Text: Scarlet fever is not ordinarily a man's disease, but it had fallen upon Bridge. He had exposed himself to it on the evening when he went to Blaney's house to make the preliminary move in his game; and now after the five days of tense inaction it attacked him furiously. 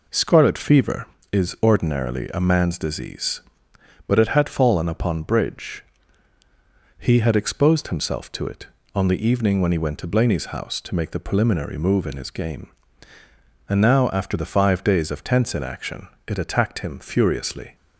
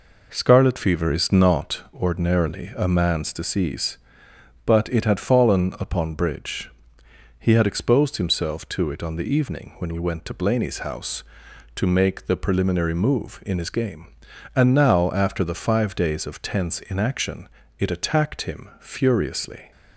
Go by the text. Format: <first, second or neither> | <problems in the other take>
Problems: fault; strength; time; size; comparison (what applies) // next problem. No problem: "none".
second | skips "not"; at 1.5 s // pauses between "inaction" and "it"; slight; at 16.0 s; 0.22 s long; slight in the second